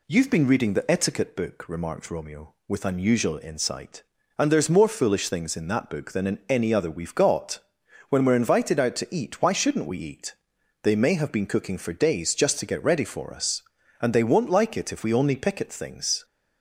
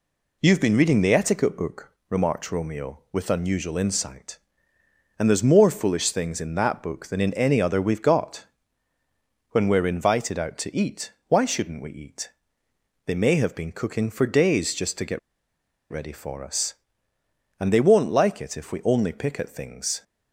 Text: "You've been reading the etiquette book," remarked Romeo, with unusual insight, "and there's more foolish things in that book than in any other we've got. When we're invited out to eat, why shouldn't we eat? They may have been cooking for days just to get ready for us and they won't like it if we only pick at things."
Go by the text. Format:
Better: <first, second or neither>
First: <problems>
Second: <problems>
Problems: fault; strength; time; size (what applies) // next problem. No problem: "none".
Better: first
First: none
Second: pauses between "get" and "ready"; noticeable; at 15.1 s; 0.71 s long